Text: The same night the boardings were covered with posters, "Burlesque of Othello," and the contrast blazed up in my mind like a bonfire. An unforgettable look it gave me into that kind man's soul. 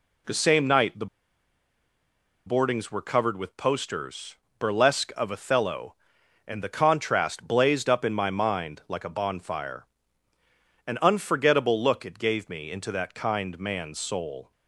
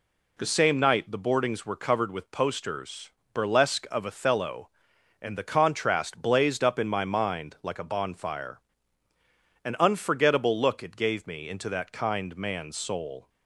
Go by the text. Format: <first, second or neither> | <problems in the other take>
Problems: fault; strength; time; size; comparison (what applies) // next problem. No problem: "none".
second | pauses between "the" and "boardings"; strong; at 1.0 s; 1.4 s long